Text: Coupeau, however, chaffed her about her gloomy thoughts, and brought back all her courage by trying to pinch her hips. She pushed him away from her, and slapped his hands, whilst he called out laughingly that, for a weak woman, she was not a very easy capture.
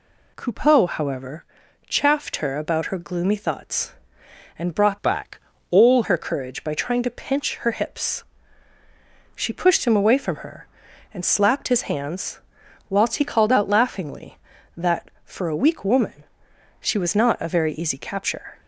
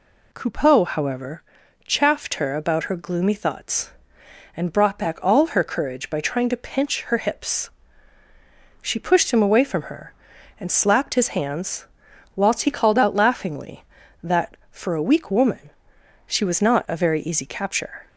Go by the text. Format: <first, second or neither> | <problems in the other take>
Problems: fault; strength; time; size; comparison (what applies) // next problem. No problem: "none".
second | changes voice from "back" to "all"; from 5.0 to 6.0 s; 1.0 s long // pauses between "back" and "all"; slight; at 5.3 s; 0.32 s long